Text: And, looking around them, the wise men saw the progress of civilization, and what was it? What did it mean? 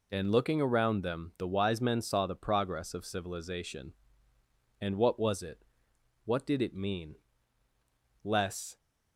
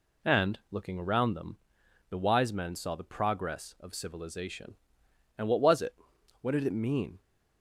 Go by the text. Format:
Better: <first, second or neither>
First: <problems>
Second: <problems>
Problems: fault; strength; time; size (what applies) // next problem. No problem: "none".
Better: second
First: goes on to say "Less"; from 8.2 s on; 0.56 s long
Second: none